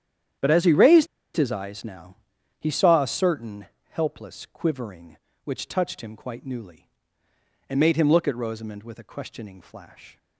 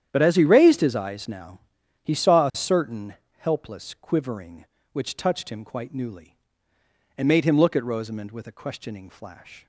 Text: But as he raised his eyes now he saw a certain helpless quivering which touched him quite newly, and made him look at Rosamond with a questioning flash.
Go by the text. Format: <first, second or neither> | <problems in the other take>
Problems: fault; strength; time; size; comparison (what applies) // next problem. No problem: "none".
second | starts louder than the rest; strong; until 1.6 s; 9.5 dB; strong in the second // pauses between "raised" and "his"; slight; at 1.0 s; 0.29 s long // pauses between "now" and "he"; at 2.1 s; 0.42 s long; also in the second // pauses between "certain" and "helpless"; slight; at 3.6 s; 0.26 s long; slight in the second